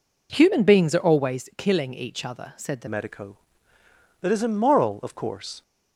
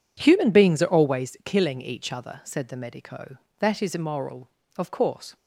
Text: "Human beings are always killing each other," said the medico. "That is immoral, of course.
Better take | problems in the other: second | changes voice at "medico"; from 2.8 s on; 2.8 s long

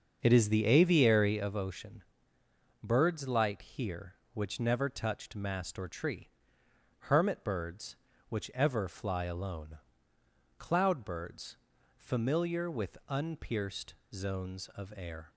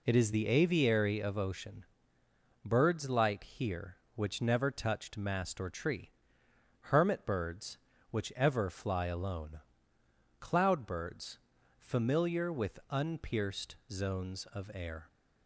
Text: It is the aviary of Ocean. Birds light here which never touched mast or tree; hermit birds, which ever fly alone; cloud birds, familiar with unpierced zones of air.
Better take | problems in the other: second | starts louder than the rest; until 1.6 s; 6.5 dB // pauses between "unpierced" and "zones"; slight; at 13.9 s; 0.18 s long

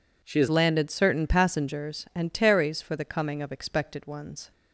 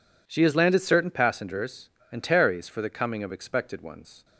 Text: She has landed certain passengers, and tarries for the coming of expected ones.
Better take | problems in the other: second | changes voice at "landed"; from 0.4 s on; 4.1 s long

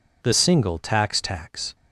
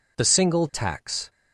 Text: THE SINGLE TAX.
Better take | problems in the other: second | says "TAX" twice; at 1.2 s

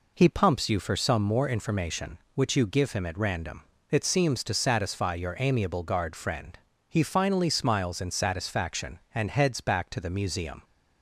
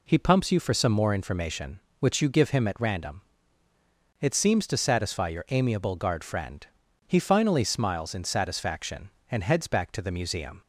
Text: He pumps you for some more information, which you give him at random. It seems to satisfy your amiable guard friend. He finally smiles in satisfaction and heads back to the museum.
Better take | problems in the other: neither | none

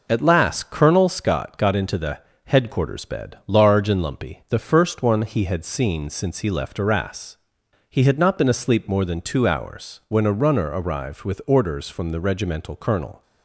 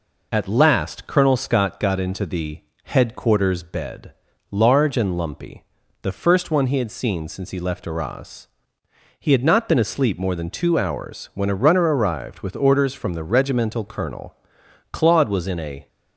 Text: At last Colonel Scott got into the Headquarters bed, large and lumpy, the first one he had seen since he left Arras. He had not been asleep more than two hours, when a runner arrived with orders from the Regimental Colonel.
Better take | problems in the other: first | pauses between "the" and "Headquarters"; slight; at 2.6 s; 0.22 s long; slight in the first // goes on to say "Claude was in a"; noticeable; from 14.9 s on; 0.96 s long

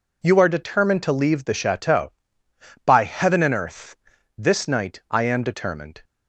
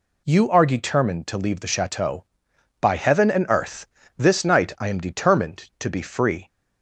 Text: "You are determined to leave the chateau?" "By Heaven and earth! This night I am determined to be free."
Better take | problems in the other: second | stops before "to be free"; at 6.0 s

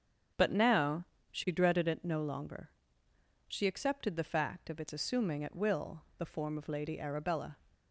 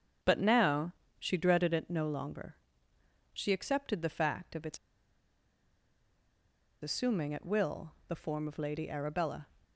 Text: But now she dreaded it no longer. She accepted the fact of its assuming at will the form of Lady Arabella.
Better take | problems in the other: first | starts louder than the rest; strong; until 1.4 s; 7.5 dB; strong in the first // pauses between "now" and "she"; slight; at 0.9 s; 0.24 s long; slight in the first // pauses between "its" and "assuming"; strong; at 4.7 s; 2.0 s long // pauses between "will" and "the"; slight; at 7.9 s; 0.16 s long; slight in the first

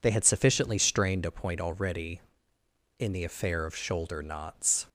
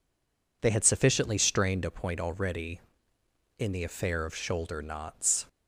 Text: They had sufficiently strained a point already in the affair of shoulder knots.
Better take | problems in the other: first | stays silent before the first word; slight; until 0.6 s; 0.6 s long

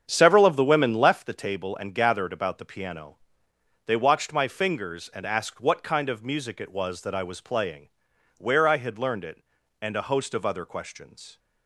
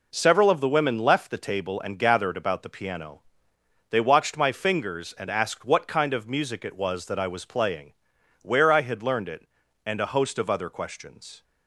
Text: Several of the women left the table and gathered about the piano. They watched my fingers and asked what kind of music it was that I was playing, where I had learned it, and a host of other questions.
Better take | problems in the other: second | starts louder than the rest; strong; until 1.2 s; 8 dB

